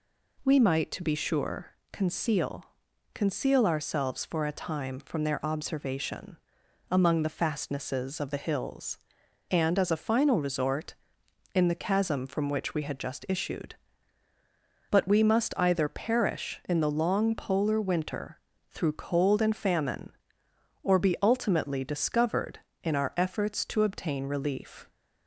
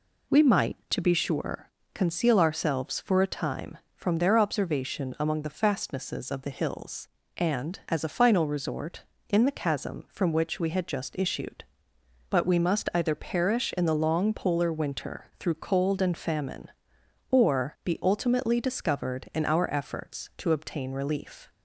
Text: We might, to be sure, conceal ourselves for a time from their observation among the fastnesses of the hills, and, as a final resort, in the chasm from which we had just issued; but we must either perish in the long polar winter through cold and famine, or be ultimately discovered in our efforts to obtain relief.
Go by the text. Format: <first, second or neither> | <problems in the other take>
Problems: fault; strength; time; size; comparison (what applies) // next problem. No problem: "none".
second | says "conceal" twice; at 3.1 s // pauses between "observation" and "among"; noticeable; at 6.3 s; 0.54 s long // pauses between "winter" and "through"; slight; at 18.3 s; 0.30 s long